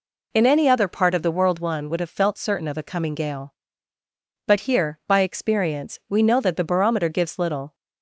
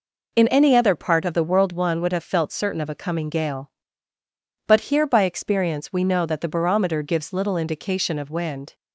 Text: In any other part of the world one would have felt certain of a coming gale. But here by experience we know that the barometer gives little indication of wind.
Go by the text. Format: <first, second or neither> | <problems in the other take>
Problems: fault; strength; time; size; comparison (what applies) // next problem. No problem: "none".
second | stops before "indication of wind"; at 7.7 s